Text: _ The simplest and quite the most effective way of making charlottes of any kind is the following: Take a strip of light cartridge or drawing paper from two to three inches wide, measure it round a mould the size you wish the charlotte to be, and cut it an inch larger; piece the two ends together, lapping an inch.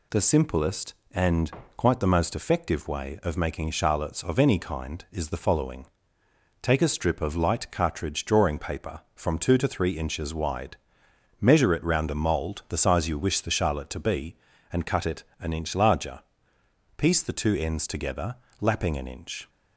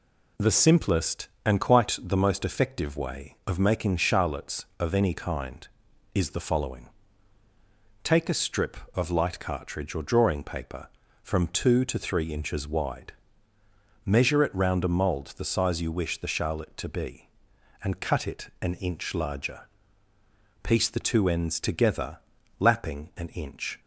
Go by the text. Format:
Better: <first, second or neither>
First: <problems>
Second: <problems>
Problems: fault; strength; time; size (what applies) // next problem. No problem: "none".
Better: second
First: pauses between "and" and "quite"; slight; at 1.5 s; 0.26 s long // skips "or"; at 8.2 s // pauses between "it" and "an"; slight; at 15.2 s; 0.16 s long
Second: none